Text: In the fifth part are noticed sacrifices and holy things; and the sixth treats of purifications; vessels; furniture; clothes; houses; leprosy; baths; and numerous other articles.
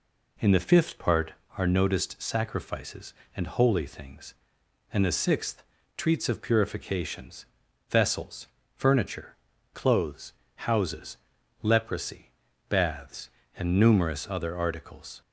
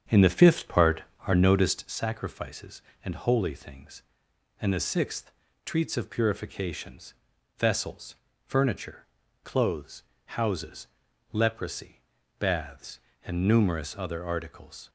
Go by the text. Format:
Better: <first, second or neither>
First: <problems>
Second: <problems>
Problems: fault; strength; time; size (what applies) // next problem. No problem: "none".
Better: first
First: pauses between "sixth" and "treats"; slight; at 5.6 s; 0.34 s long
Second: starts louder than the rest; strong; until 2.0 s; 8 dB // pauses between "sixth" and "treats"; slight; at 5.3 s; 0.34 s long